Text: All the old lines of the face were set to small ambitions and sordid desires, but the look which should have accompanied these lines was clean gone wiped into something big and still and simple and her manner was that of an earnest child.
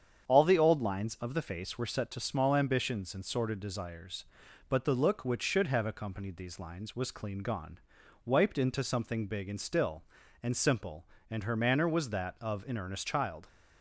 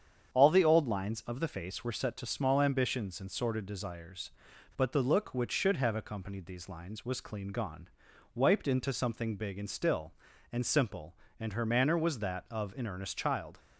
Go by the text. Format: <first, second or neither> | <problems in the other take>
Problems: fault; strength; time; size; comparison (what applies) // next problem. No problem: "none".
neither | starts louder than the rest; strong; the same in both // pauses between "gone" and "wiped"; noticeable; the same in both